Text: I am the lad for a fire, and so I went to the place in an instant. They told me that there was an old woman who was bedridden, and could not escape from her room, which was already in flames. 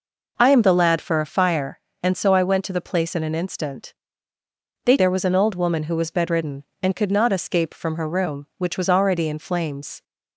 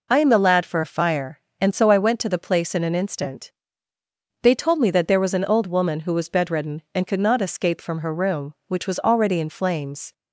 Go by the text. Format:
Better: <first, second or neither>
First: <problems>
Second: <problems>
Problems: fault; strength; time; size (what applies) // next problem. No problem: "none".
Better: second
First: skips "told me that"; at 4.9 s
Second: none